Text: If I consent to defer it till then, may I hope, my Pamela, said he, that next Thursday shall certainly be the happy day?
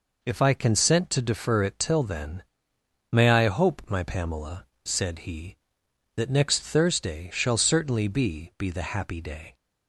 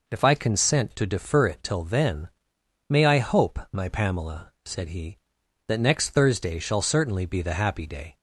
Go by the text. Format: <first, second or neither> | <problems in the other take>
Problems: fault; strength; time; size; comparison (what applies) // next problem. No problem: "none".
second | says "be" twice; at 8.5 s